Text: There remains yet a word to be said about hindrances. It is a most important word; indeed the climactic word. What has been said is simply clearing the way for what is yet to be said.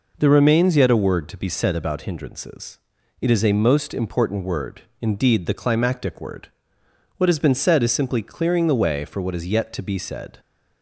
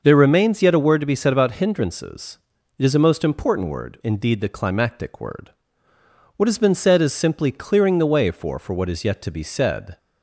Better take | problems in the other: first | says "for" twice; at 8.5 s

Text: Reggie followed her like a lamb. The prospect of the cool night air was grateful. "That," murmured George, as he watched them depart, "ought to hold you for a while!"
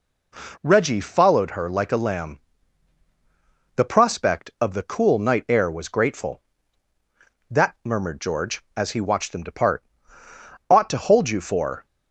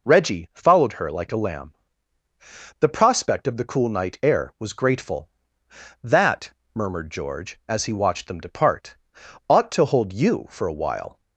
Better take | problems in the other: second | stops before "a while"; at 11.8 s

